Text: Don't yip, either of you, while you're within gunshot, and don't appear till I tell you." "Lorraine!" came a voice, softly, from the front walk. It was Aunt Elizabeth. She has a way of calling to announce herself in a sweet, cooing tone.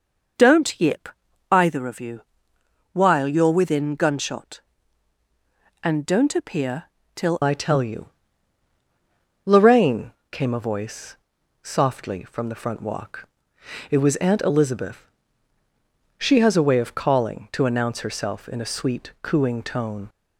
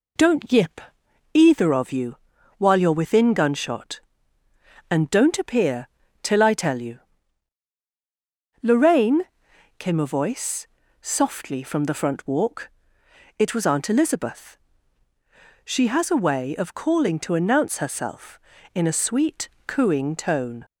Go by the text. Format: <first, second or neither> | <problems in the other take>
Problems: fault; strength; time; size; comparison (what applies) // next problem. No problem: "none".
second | pauses between "appear" and "till"; slight; at 6.8 s; 0.30 s long; slight in the second // changes voice at "I"; from 7.4 s on; 12.6 s long